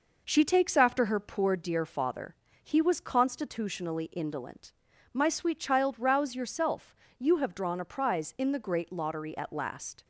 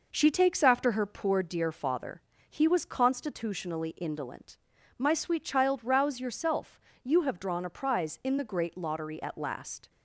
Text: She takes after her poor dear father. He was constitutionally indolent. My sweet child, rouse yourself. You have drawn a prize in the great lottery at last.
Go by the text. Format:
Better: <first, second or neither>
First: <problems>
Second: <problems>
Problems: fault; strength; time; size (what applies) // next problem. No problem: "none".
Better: neither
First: none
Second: none